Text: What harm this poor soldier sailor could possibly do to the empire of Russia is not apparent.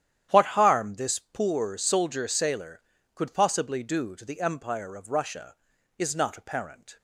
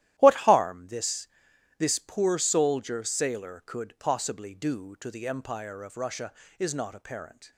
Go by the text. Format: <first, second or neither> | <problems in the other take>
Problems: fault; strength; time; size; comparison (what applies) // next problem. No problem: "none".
first | starts louder than the rest; strong; until 1.1 s; 13.5 dB; strong in the first // says "this" twice; at 1.7 s